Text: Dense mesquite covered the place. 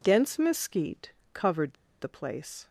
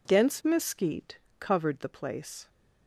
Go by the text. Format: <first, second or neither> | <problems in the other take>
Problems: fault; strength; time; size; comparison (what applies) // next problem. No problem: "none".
second | pauses between "mesquite" and "covered"; slight; at 1.1 s; 0.20 s long; slight in the second // pauses between "covered" and "the"; slight; at 1.7 s; 0.27 s long